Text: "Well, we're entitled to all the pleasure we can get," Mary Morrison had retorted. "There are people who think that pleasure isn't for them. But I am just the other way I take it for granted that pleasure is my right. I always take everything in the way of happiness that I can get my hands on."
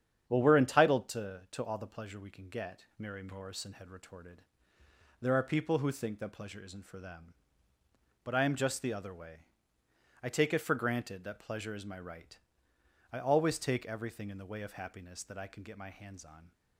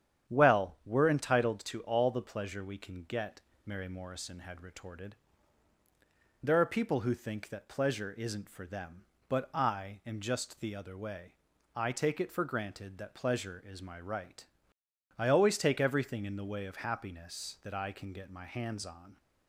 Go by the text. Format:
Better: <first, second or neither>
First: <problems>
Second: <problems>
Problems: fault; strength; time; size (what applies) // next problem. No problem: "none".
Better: second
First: starts louder than the rest; strong; until 1.3 s; 8.5 dB // says "to" twice; at 1.4 s // pauses between "way" and "I"; noticeable; at 9.4 s; 0.76 s long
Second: starts louder than the rest; strong; until 1.3 s; 9 dB // pauses between "way" and "I"; at 11.3 s; 0.42 s long